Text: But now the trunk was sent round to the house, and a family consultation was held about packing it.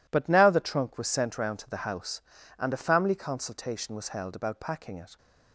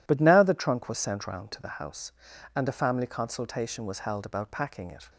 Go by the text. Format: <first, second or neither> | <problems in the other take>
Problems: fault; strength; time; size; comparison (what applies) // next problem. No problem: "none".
neither | none